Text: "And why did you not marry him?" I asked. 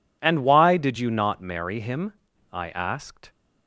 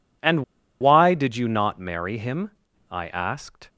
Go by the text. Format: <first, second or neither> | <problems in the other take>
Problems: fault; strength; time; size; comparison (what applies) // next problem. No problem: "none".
first | pauses between "And" and "why"; at 0.4 s; 0.36 s long